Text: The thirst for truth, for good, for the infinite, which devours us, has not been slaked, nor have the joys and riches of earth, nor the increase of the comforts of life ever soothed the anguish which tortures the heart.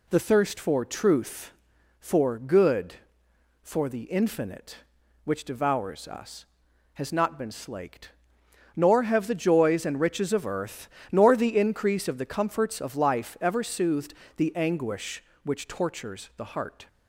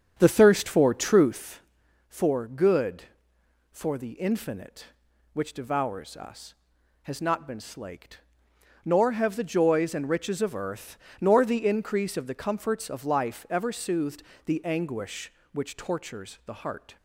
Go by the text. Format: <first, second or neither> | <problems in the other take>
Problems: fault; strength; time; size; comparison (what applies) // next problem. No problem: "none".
first | starts louder than the rest; strong; until 1.4 s; 8 dB // pauses between "soothed" and "the"; slight; at 14.2 s; 0.24 s long; slight in the first